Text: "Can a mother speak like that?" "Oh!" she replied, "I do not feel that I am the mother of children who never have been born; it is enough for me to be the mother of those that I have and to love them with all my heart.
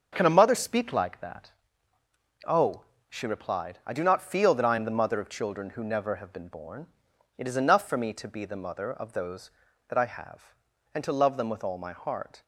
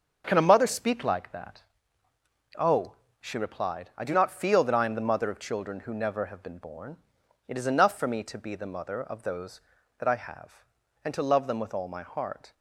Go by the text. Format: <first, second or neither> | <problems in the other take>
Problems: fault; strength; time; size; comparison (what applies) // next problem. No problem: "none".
neither | starts louder than the rest; the same in both